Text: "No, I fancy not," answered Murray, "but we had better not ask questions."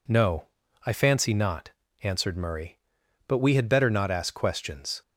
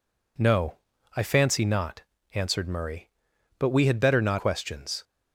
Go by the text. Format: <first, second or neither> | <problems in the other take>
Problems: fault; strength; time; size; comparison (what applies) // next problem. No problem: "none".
first | skips "ask"; at 4.3 s